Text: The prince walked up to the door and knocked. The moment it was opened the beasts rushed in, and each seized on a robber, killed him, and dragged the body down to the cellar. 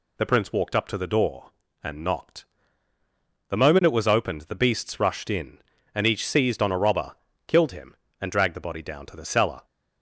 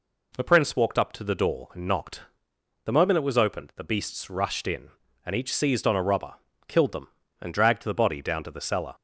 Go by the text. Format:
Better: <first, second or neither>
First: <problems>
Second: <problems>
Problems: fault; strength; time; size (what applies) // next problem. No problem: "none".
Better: first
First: none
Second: says "them" for "him"; at 6.9 s